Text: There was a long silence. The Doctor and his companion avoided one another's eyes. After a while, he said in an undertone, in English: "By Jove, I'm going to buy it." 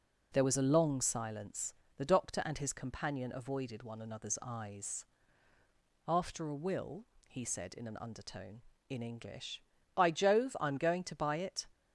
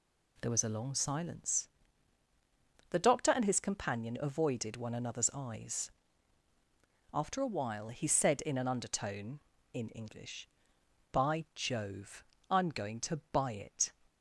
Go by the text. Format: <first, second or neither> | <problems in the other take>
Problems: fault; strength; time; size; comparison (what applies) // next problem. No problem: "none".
second | says "will" for "while"; at 6.5 s